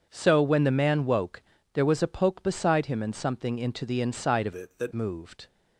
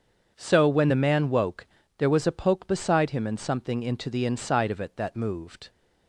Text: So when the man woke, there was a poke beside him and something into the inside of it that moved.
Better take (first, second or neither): second